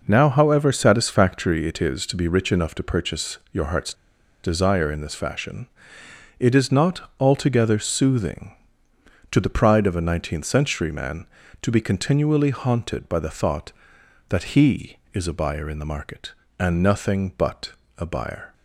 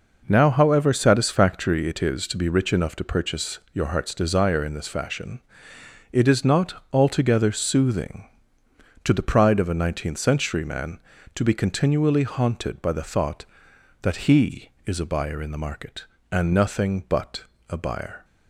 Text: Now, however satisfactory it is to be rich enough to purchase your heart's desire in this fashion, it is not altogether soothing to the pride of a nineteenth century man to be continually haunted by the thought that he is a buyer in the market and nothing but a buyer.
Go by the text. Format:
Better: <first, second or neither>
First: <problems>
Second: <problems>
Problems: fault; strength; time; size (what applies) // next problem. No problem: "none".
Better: second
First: pauses between "purchase" and "your"; slight; at 3.3 s; 0.16 s long // pauses between "heart's" and "desire"; noticeable; at 3.9 s; 0.51 s long // pauses between "but" and "a"; slight; at 17.7 s; 0.26 s long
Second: pauses between "purchase" and "your"; slight; at 3.5 s; 0.16 s long // pauses between "but" and "a"; slight; at 17.4 s; 0.26 s long